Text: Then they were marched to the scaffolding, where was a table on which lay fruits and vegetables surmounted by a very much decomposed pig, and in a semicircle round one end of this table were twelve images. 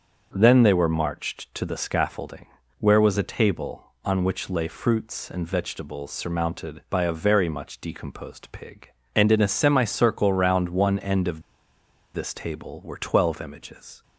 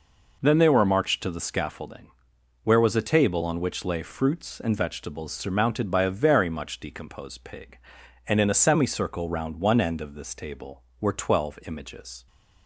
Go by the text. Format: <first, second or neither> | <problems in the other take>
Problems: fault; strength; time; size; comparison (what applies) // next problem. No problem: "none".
second | starts louder than the rest; until 1.3 s; 7 dB // pauses between "of" and "this"; noticeable; at 11.4 s; 0.72 s long